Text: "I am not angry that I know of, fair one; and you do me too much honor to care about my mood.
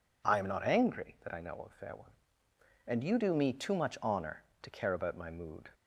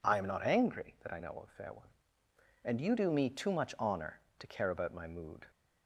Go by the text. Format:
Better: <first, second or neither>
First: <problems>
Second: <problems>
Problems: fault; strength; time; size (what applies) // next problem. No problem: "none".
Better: neither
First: none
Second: none